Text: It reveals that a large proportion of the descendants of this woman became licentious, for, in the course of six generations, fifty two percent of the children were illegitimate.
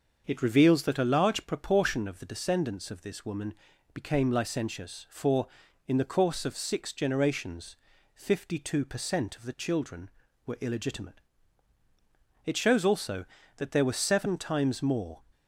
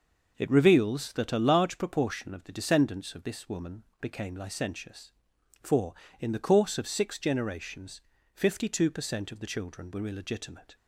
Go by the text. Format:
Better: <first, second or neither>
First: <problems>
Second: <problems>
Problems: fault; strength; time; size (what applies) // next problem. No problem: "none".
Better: second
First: starts louder than the rest; until 1.2 s; 6.5 dB // pauses between "woman" and "became"; at 3.5 s; 0.38 s long // goes on to say "It shows also that there were seven times more"; strong; from 12.4 s on; 2.7 s long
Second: pauses between "woman" and "became"; slight; at 3.8 s; 0.18 s long